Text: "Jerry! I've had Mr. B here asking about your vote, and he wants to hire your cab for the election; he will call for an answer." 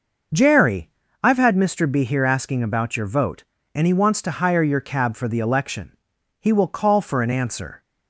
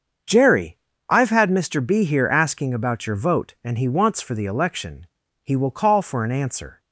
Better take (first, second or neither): first